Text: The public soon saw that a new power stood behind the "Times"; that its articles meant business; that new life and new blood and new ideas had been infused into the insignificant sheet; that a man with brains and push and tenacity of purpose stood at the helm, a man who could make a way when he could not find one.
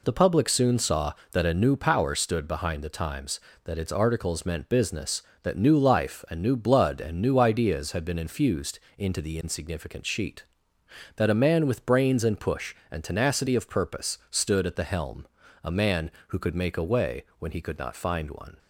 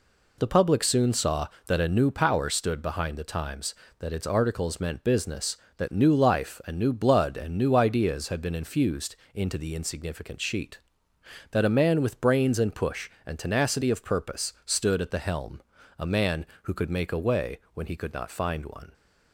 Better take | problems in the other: neither | pauses between "infused" and "into"; slight; the same in both // pauses between "way" and "when"; slight; the same in both

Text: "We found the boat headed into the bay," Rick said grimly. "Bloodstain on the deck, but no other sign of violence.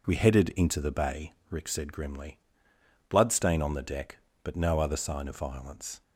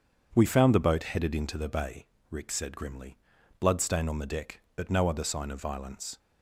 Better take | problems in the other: second | skips "found the boat"; at 0.1 s

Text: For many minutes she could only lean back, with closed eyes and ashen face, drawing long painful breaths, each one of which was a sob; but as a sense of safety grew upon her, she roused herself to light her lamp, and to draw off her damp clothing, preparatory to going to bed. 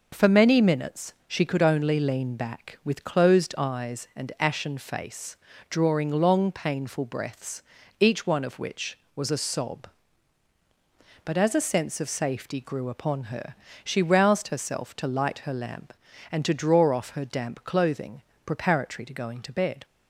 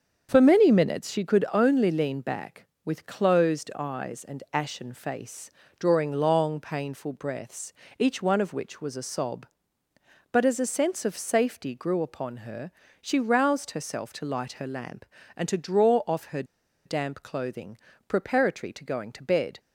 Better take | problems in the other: first | starts louder than the rest; strong; until 1.3 s; 7 dB // pauses between "her" and "damp"; at 16.4 s; 0.41 s long

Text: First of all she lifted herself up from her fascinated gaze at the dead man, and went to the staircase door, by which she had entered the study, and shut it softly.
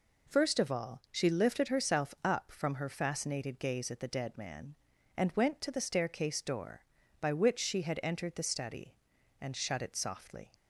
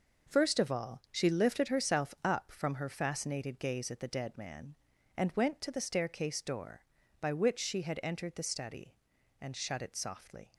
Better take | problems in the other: first | gets quieter; strong; throughout; 8.5 dB

